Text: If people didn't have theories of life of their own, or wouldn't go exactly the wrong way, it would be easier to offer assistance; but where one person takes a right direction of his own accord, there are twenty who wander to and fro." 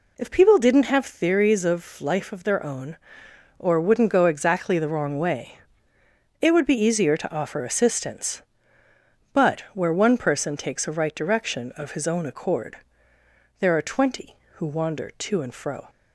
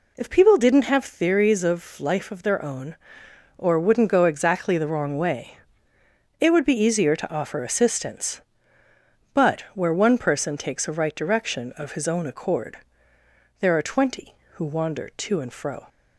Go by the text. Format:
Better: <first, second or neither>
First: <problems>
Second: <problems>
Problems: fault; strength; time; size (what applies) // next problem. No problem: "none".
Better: neither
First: none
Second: none